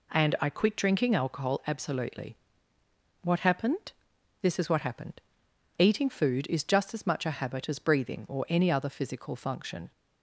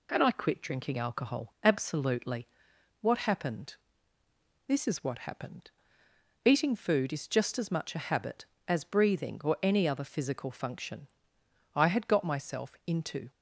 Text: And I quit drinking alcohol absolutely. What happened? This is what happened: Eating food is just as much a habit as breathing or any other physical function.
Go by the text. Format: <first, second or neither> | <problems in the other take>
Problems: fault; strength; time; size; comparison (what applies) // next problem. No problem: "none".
first | goes on to say "I had got myself into"; from 11.7 s on; 1.5 s long